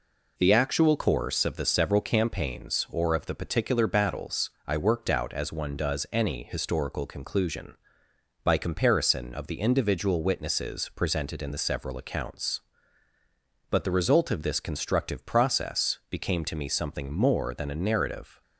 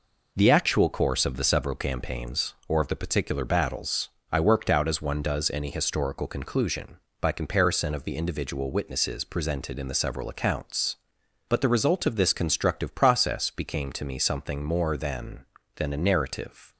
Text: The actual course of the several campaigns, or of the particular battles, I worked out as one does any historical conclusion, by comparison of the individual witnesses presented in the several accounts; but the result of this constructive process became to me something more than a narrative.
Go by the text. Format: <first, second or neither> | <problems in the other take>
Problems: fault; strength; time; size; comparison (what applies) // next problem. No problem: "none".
first | says "than" twice; at 15.7 s